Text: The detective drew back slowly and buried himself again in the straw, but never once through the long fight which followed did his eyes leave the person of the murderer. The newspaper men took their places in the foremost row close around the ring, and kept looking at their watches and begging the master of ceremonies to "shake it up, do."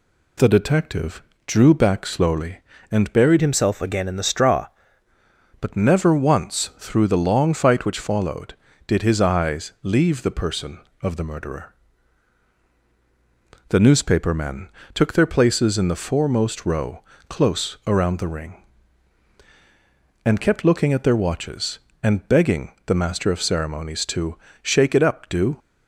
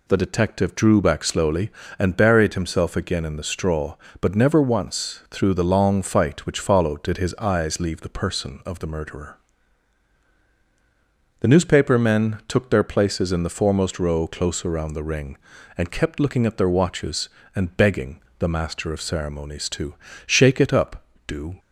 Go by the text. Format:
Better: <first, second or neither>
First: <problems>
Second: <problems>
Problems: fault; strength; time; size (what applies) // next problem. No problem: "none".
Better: second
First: pauses between "detective" and "drew"; slight; at 1.2 s; 0.26 s long // changes voice from "himself" to "straw"; from 3.4 to 4.6 s; 1.2 s long // pauses between "men" and "took"; slight; at 14.7 s; 0.24 s long // pauses between "row" and "close"; slight; at 17.0 s; 0.24 s long // pauses between "begging" and "the"; slight; at 22.7 s; 0.16 s long // pauses between "to" and "shake"; slight; at 24.3 s; 0.26 s long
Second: pauses between "begging" and "the"; slight; at 18.2 s; 0.18 s long // pauses between "to" and "shake"; slight; at 19.9 s; 0.32 s long